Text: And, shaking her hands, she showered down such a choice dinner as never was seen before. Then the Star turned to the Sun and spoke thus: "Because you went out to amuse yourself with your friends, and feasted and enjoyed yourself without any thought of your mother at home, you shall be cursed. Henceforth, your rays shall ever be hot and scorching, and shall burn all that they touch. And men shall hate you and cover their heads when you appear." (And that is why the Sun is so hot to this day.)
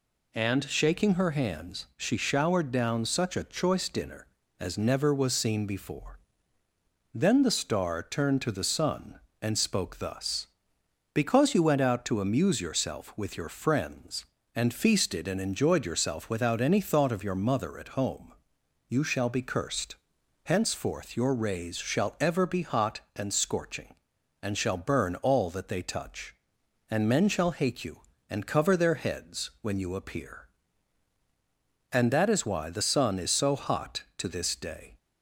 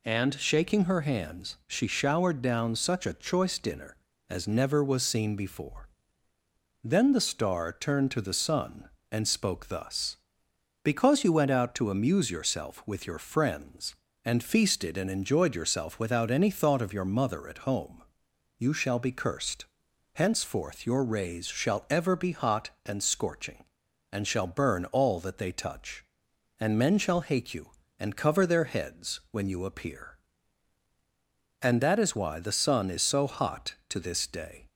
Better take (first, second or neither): neither